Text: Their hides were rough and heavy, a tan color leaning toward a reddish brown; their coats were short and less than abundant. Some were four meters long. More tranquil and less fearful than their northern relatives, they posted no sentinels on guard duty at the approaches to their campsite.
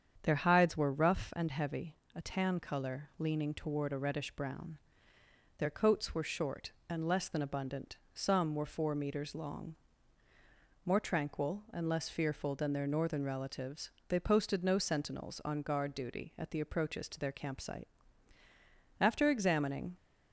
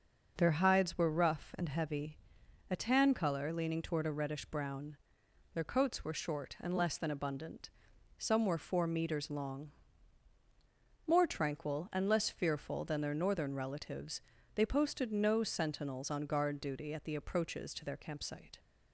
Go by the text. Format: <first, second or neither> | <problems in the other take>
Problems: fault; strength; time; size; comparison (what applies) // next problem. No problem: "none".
second | starts louder than the rest; strong; until 1.2 s; 7.5 dB // goes on to say "After examining"; noticeable; from 19.0 s on; 0.96 s long